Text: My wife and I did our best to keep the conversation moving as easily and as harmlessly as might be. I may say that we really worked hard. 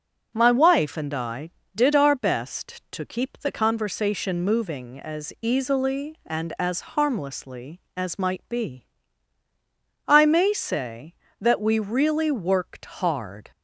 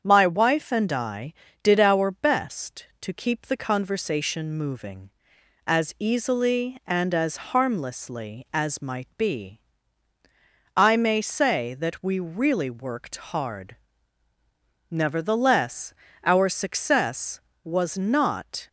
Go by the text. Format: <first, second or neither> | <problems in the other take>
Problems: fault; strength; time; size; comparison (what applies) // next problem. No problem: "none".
first | starts louder than the rest; strong; until 1.0 s; 7.5 dB // goes on to say "Nevertheless our success was not"; strong; from 14.8 s on; 3.7 s long